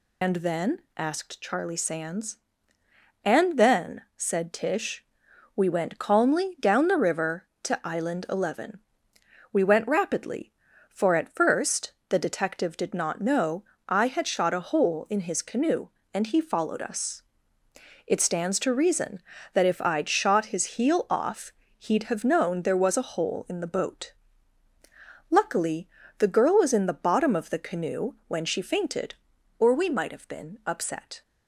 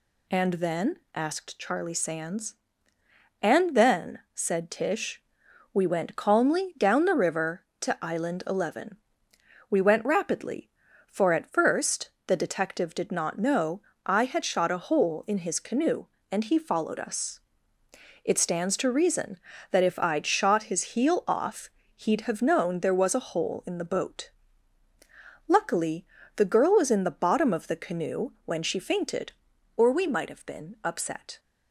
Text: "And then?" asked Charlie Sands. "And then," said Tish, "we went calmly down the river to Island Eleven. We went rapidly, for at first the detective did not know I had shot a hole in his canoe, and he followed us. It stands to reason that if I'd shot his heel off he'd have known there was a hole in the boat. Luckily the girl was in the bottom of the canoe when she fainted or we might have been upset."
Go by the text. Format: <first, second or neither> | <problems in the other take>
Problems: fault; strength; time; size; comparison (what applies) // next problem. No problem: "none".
second | loses the start of "And"; at 0.2 s; 100 ms // pauses between "first" and "the"; slight; at 11.9 s; 0.18 s long; slight in the second // pauses between "know" and "I"; slight; at 13.6 s; 0.24 s long; slight in the second // pauses between "off" and "he'd"; slight; at 21.5 s; 0.26 s long; slight in the second // pauses between "Luckily" and "the"; slight; at 25.8 s; 0.30 s long; slight in the second